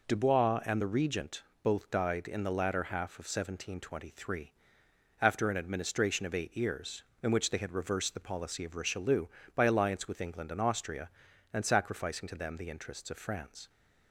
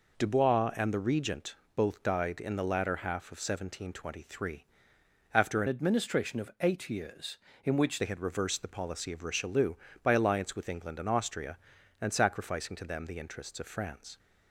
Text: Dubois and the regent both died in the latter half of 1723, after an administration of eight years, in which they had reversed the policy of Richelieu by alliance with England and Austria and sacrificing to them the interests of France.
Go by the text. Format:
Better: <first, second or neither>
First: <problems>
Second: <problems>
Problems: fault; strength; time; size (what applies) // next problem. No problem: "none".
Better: first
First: pauses between "regent" and "both"; slight; at 1.4 s; 0.18 s long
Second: pauses between "regent" and "both"; slight; at 1.5 s; 0.18 s long // changes voice from "administration" to "which"; from 5.6 to 8.0 s; 2.4 s long